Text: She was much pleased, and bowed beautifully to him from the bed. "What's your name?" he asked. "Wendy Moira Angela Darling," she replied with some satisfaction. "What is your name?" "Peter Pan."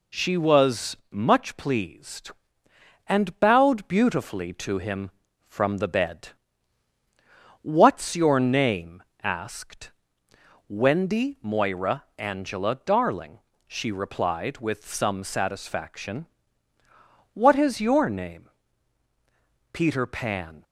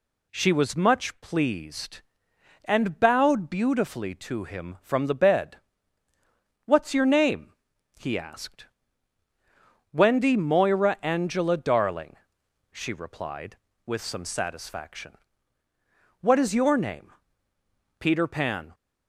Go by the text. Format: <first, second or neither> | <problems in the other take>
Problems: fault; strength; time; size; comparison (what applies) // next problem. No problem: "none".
second | skips "he"; at 9.1 s // pauses between "Moira" and "Angela"; slight; at 12.0 s; 0.16 s long